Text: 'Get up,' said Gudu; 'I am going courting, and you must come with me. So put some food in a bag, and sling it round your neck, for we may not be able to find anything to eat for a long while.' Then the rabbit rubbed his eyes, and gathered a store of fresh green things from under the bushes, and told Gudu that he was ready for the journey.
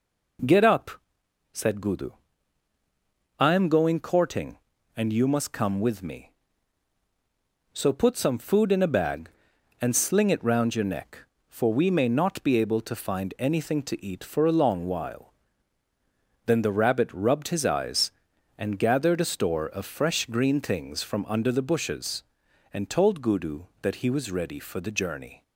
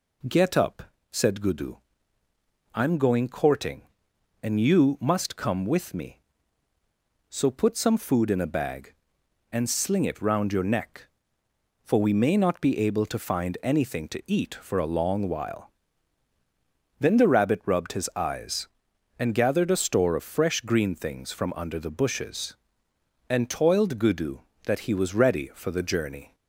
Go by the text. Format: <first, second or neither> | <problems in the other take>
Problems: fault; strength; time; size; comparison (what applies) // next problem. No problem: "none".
first | says "toiled" for "told"; at 23.4 s